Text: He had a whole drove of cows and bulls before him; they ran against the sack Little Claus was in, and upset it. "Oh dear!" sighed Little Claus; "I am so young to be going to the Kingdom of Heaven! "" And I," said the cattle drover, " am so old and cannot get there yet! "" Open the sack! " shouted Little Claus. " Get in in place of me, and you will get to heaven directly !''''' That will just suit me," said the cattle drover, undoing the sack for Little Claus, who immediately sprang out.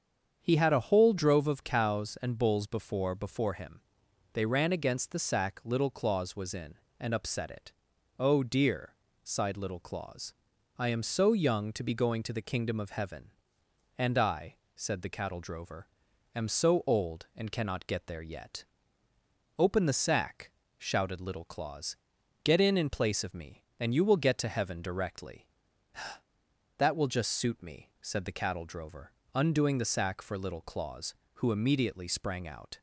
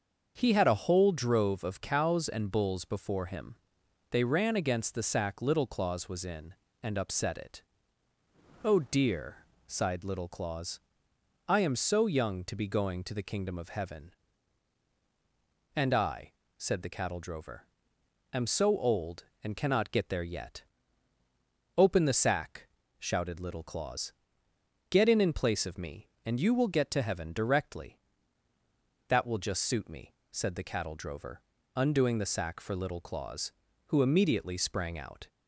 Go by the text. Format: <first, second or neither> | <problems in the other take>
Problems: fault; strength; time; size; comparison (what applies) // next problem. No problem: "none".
second | starts louder than the rest; strong; until 1.4 s; 7.5 dB; also in the second // says "before" twice; at 3.1 s